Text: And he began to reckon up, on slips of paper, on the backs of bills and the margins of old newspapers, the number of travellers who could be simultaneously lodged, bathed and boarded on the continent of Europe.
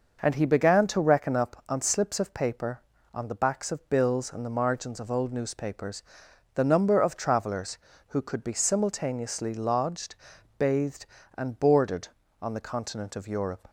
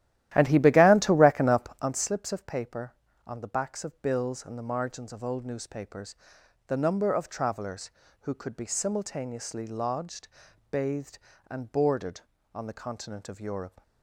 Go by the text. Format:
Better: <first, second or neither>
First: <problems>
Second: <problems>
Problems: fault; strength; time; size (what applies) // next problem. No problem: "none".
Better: first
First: none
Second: starts louder than the rest; strong; until 2.0 s; 13.5 dB